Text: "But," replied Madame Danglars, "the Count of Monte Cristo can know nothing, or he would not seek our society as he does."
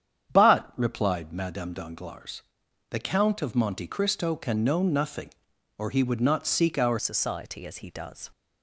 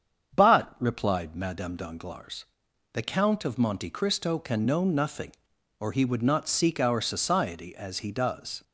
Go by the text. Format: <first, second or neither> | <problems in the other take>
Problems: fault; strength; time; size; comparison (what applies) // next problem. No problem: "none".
second | starts louder than the rest; strong; until 1.3 s; 8.5 dB; strong in the second // changes voice at "society"; from 6.9 s on; 1.4 s long